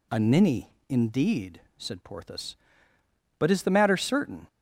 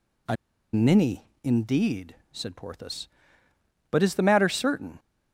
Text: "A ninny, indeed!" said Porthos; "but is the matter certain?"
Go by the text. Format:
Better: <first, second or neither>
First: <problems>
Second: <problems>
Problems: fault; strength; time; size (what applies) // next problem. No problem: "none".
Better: first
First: none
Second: pauses between "A" and "ninny"; at 0.3 s; 0.37 s long